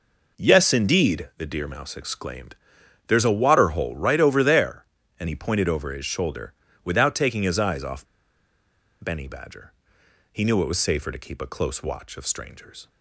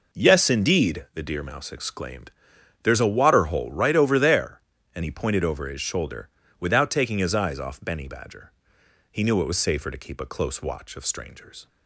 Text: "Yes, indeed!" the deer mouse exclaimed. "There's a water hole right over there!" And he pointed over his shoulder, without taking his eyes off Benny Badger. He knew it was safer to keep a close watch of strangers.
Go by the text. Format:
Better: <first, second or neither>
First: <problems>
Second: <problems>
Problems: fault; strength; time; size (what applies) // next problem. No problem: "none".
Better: second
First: pauses between "off" and "Benny"; noticeable; at 8.0 s; 0.97 s long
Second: none